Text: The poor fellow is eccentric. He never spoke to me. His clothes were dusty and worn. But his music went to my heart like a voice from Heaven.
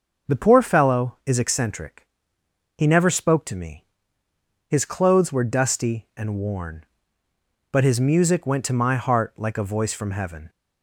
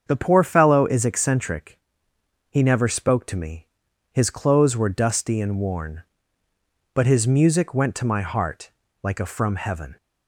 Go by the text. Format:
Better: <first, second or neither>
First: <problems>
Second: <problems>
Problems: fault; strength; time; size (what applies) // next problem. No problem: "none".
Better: first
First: starts louder than the rest; noticeable; until 1.3 s; 6 dB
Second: starts louder than the rest; strong; until 1.0 s; 7 dB // pauses between "heart" and "like"; slight; at 8.7 s; 0.32 s long // skips "voice"; at 9.2 s